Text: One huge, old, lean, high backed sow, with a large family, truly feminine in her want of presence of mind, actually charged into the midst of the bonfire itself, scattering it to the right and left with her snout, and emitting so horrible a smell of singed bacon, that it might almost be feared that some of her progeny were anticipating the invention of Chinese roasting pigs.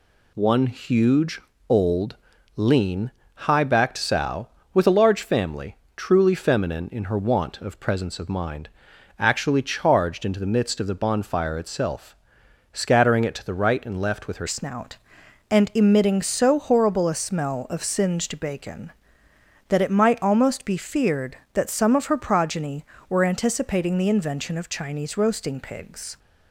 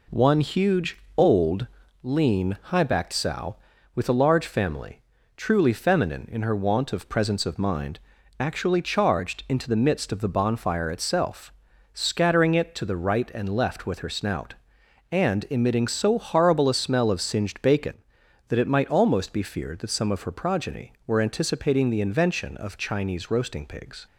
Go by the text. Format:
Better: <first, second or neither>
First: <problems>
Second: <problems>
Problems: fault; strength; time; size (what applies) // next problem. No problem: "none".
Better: second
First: changes voice at "snout"; from 14.4 s on; 11.7 s long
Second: none